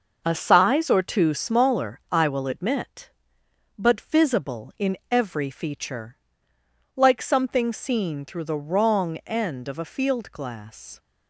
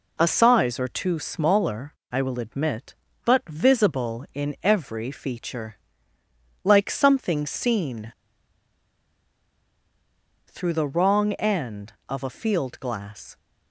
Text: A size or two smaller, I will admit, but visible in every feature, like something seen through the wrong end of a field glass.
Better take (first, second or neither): first